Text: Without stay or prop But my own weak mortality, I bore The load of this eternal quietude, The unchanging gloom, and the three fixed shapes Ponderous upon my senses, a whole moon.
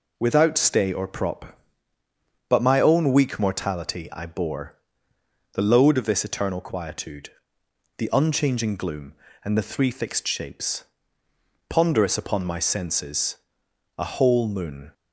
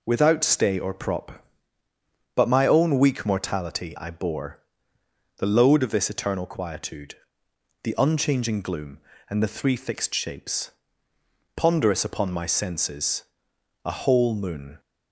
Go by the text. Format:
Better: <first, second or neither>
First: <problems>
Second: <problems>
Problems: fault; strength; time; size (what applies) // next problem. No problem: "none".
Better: neither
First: pauses between "bore" and "The"; noticeable; at 4.7 s; 0.78 s long // pauses between "shapes" and "Ponderous"; noticeable; at 10.8 s; 0.84 s long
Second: pauses between "bore" and "The"; noticeable; at 4.5 s; 0.78 s long // pauses between "shapes" and "Ponderous"; noticeable; at 10.6 s; 0.84 s long